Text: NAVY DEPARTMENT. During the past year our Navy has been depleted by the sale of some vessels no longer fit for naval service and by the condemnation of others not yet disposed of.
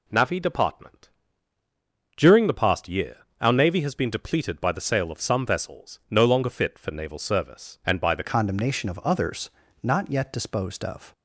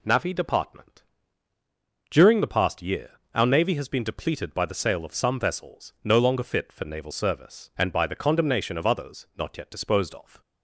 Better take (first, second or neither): second